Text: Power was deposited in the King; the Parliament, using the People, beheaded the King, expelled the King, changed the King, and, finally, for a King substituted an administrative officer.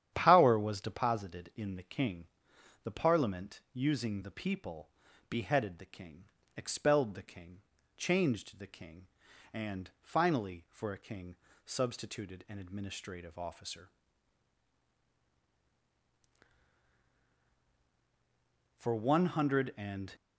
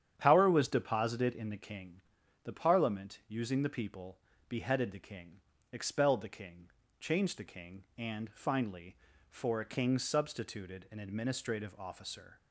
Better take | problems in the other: second | starts louder than the rest; strong; until 1.1 s; 10 dB; strong in the second // pauses between "King" and "substituted"; slight; at 11.3 s; 0.30 s long // goes on to say "For one hundred and"; from 18.7 s on; 1.3 s long

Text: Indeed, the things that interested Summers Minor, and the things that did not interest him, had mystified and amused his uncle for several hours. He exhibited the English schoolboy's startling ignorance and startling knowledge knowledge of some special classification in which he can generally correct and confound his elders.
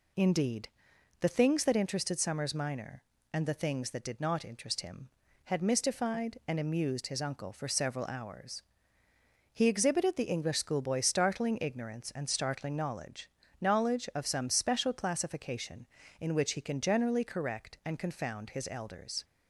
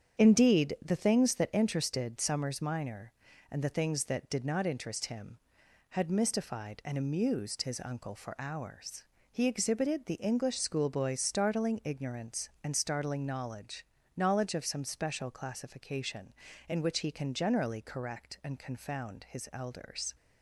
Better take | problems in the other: first | starts louder than the rest; strong; until 1.2 s; 8 dB // skips "several"; at 8.3 s // pauses between "knowledge" and "knowledge"; slight; at 13.8 s; 0.34 s long; slight in the first

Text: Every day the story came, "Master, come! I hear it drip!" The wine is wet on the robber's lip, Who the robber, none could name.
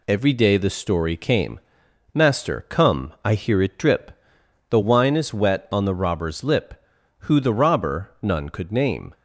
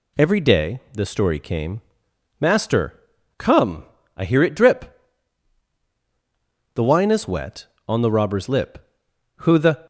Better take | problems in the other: first | stops before "robber none could name"; at 9.8 s

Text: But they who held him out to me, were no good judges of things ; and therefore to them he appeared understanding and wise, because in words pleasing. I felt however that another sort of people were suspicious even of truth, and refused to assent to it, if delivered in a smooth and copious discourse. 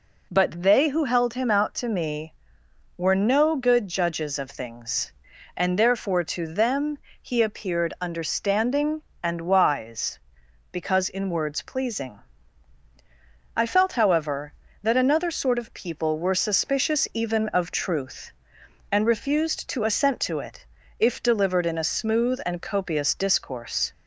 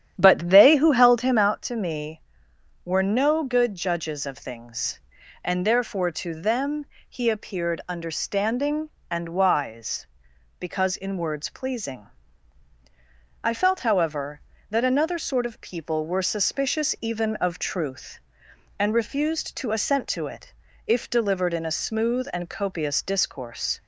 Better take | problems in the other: first | starts louder than the rest; strong; until 1.5 s; 10 dB // pauses between "them" and "he"; slight; at 6.8 s; 0.24 s long; slight in the first

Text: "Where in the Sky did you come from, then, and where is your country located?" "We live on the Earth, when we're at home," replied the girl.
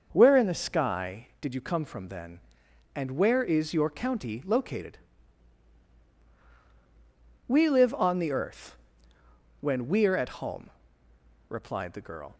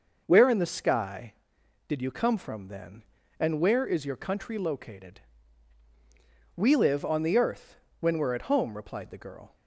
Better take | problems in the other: second | starts louder than the rest; noticeable; until 1.1 s; 6 dB // says "county" for "country"; at 3.8 s

